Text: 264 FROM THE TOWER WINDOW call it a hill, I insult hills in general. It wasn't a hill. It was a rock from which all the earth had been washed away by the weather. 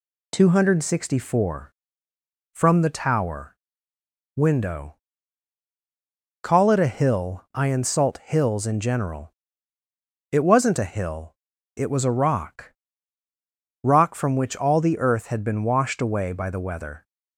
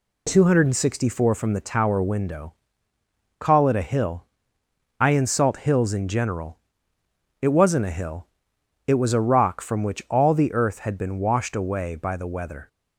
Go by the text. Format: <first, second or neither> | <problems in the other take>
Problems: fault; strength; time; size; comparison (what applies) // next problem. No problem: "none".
second | pauses between "TOWER" and "WINDOW"; noticeable; at 3.5 s; 0.80 s long // pauses between "WINDOW" and "call"; strong; at 4.9 s; 1.4 s long; noticeable in the second // says "rock" twice; at 13.8 s